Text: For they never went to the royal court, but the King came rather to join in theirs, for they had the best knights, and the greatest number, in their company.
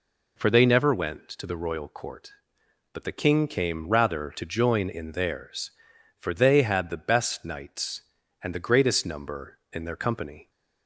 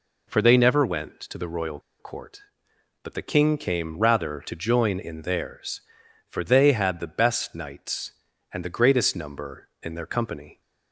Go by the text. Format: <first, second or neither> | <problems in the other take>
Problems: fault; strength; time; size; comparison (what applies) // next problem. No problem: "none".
first | pauses between "royal" and "court"; slight; at 1.7 s; 0.20 s long